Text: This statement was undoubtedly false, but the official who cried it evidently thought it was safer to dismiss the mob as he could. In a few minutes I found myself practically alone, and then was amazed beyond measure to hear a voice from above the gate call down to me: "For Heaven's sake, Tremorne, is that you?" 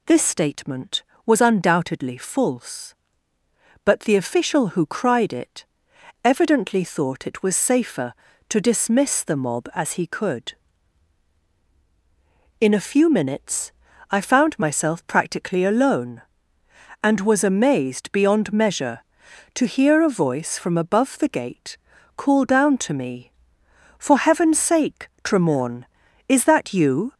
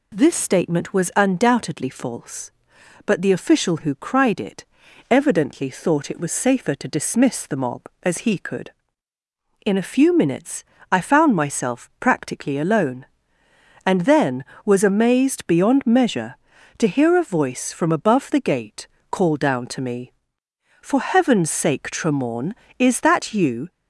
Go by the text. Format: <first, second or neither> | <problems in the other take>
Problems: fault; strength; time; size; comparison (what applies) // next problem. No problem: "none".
second | pauses between "it" and "evidently"; noticeable; at 5.6 s; 0.58 s long; noticeable in the second // pauses between "minutes" and "I"; at 13.7 s; 0.38 s long; slight in the second // skips "then"; at 17.1 s // pauses between "gate" and "call"; at 21.7 s; 0.40 s long; slight in the second